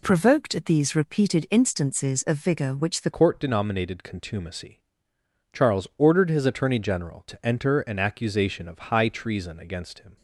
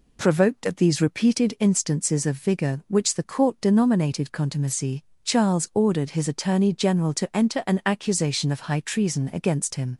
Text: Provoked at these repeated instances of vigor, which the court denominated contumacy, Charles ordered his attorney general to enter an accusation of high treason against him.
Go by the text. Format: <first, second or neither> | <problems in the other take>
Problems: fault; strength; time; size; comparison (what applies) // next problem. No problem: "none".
second | changes voice at "court"; from 3.1 s on; 7.0 s long